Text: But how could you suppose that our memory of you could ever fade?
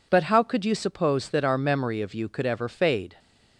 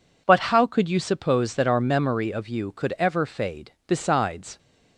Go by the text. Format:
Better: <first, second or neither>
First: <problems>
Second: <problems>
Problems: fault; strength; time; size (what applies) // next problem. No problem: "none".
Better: first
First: none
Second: goes on to say "Besides"; noticeable; from 3.8 s on; 0.70 s long